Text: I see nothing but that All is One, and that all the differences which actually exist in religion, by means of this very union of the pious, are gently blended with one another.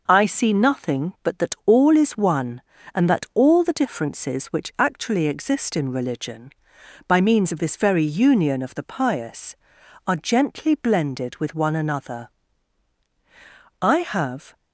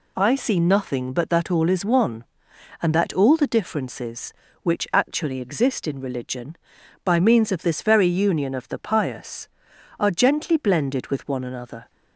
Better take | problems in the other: second | goes on to say "I have"; noticeable; from 13.8 s on; 0.74 s long

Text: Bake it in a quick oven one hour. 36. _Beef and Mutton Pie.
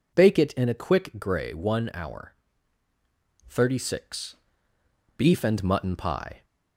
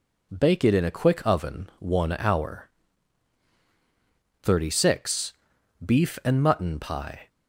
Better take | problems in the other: second | says "grey" for "oven"; at 1.1 s

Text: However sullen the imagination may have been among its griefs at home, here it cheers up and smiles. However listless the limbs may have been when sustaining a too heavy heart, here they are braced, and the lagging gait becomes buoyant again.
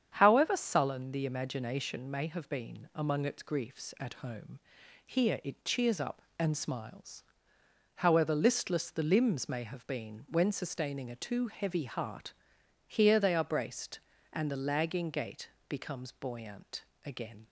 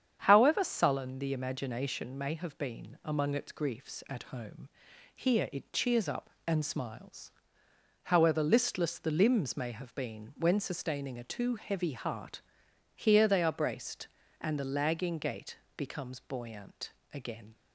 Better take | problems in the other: neither | starts louder than the rest; strong; the same in both // pauses between "gait" and "becomes"; slight; the same in both // pauses between "buoyant" and "again"; slight; the same in both

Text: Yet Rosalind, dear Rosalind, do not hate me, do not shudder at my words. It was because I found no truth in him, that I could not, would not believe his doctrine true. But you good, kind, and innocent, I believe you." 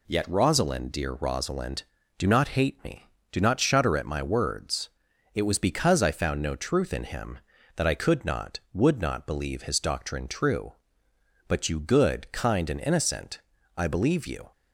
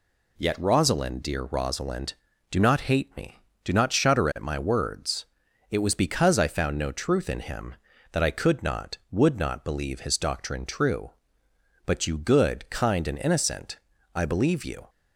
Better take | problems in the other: neither | none

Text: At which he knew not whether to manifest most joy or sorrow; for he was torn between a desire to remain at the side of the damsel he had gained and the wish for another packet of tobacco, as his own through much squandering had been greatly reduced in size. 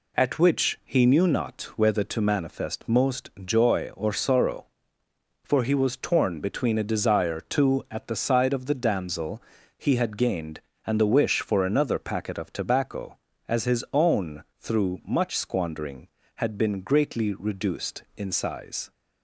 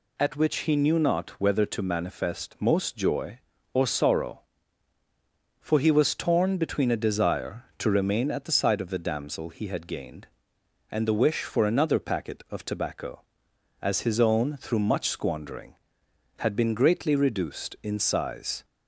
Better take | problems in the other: second | skips "remain"; at 7.8 s // pauses between "damsel" and "he"; slight; at 9.4 s; 0.34 s long

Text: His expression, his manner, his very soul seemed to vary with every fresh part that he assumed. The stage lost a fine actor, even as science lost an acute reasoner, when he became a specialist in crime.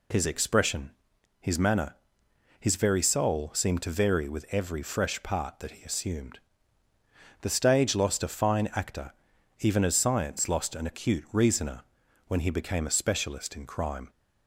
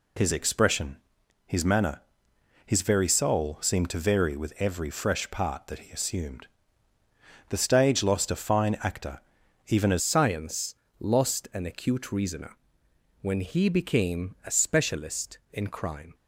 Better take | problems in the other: first | changes voice at "science"; from 9.9 s on; 6.2 s long // pauses between "science" and "lost"; slight; at 10.7 s; 0.24 s long

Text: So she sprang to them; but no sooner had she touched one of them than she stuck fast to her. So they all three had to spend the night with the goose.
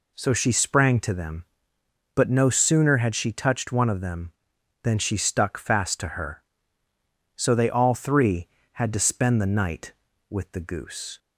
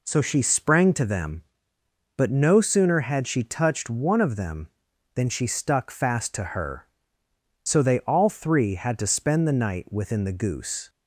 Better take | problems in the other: first | says "within" for "with"; at 9.9 s

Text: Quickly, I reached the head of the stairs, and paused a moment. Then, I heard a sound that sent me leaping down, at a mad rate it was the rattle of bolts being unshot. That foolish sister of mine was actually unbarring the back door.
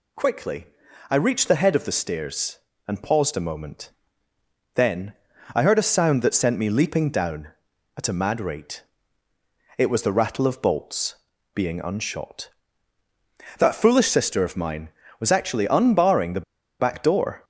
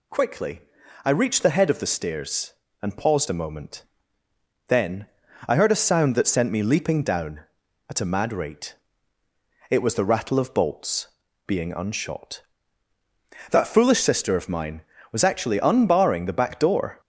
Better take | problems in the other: second | pauses between "rate" and "it"; noticeable; at 8.8 s; 0.94 s long; noticeable in the second // pauses between "bolts" and "being"; at 11.1 s; 0.38 s long; also in the second // pauses between "the" and "back"; at 16.4 s; 0.37 s long

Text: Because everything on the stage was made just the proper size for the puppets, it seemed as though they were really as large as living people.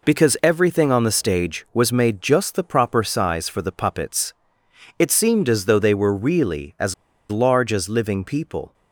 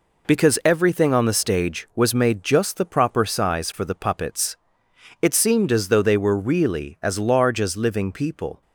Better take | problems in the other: second | pauses between "as" and "large"; slight; at 6.9 s; 0.35 s long

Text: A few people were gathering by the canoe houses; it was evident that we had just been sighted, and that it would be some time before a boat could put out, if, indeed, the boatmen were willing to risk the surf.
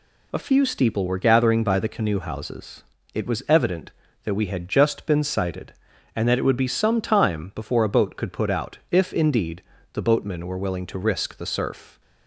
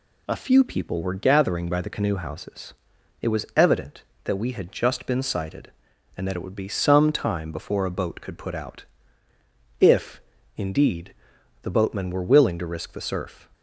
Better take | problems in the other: second | says "steeple" for "people"; at 0.6 s

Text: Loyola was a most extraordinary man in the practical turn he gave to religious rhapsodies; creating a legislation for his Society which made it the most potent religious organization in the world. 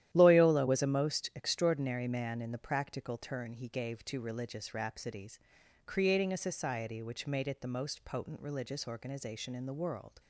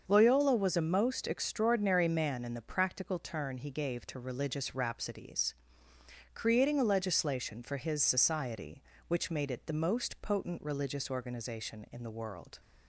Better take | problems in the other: second | starts louder than the rest; strong; until 1.1 s; 12 dB; also in the second // skips "legislation for his"; at 6.3 s

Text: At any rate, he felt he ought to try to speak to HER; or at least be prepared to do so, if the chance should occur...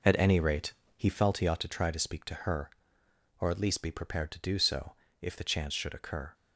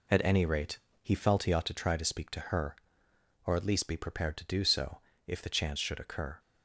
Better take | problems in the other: second | starts louder than the rest; noticeable; until 1.2 s; 5 dB

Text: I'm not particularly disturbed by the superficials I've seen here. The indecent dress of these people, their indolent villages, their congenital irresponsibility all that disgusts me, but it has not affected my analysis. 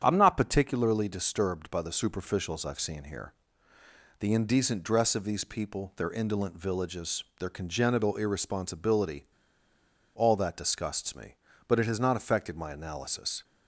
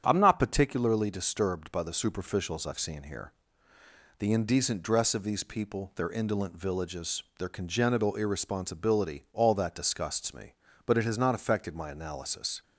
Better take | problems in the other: second | starts louder than the rest; strong; until 1.0 s; 8.5 dB; strong in the second // pauses between "irresponsibility" and "all"; noticeable; at 9.2 s; 0.87 s long

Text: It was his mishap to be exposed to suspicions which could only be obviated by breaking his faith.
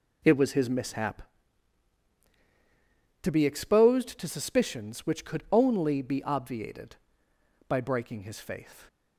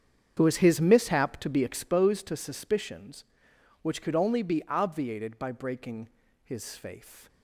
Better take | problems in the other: first | starts louder than the rest; strong; until 1.9 s; 8 dB // pauses between "breaking" and "his"; slight; at 6.0 s; 0.36 s long

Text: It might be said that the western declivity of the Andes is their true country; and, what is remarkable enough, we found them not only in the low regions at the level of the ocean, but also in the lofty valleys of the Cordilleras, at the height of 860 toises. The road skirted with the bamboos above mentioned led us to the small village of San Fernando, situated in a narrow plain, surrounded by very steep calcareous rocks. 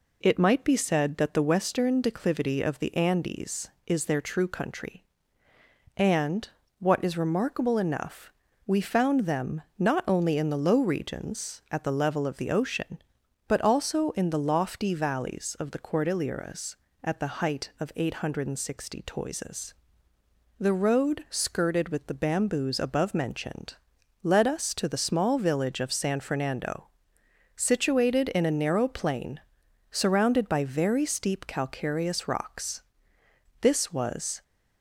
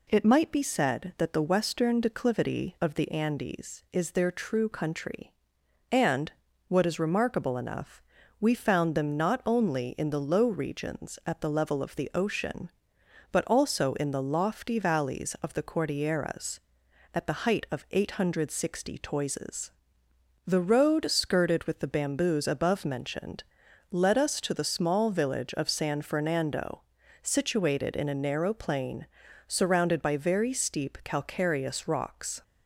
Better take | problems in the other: second | pauses between "them" and "not"; slight; at 9.6 s; 0.16 s long // pauses between "mentioned" and "led"; noticeable; at 23.7 s; 0.48 s long; noticeable in the second // goes on to say "This was"; noticeable; from 33.6 s on; 0.80 s long

